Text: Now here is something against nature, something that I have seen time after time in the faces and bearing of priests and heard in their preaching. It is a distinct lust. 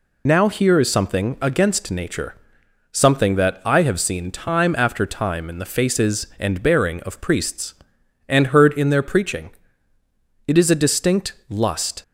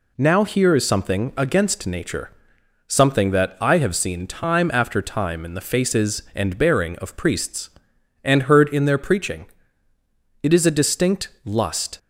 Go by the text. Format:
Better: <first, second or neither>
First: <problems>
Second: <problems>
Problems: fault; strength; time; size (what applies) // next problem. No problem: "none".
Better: second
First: loses the start of "Now"; at 0.2 s; 50 ms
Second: none